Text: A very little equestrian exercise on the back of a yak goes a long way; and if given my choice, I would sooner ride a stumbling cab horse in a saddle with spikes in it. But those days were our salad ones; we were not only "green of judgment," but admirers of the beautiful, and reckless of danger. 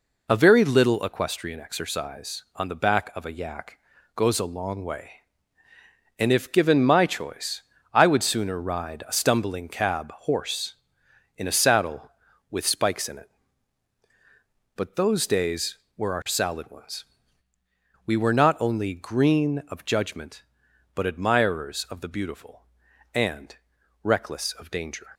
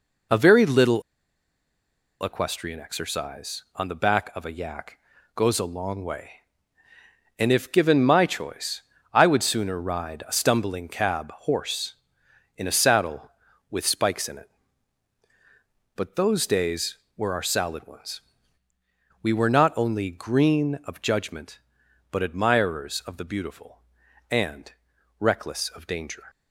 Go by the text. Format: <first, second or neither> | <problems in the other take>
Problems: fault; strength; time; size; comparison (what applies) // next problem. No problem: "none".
first | pauses between "little" and "equestrian"; at 1.0 s; 1.2 s long // pauses between "yak" and "goes"; at 4.9 s; 0.40 s long; also in the first // pauses between "and" and "reckless"; noticeable; at 24.7 s; 0.48 s long; noticeable in the first